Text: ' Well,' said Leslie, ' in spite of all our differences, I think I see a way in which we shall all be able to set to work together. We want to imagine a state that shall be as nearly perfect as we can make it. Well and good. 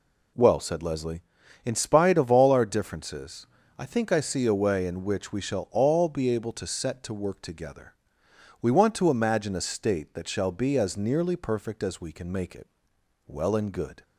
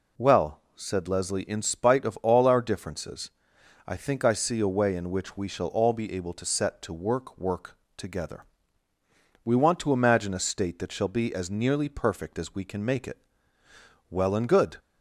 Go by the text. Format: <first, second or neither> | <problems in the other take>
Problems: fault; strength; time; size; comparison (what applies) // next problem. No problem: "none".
first | says "work" twice; at 7.3 s